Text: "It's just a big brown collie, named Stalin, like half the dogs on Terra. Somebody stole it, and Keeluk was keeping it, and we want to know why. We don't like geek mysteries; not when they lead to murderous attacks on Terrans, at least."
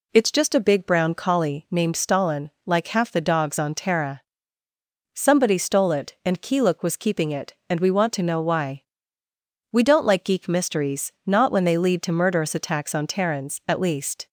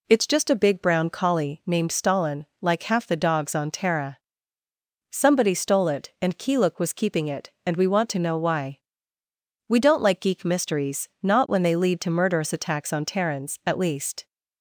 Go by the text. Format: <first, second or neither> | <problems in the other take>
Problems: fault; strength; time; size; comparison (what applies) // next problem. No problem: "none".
neither | none